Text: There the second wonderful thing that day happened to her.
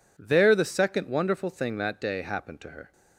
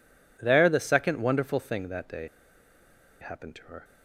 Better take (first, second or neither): first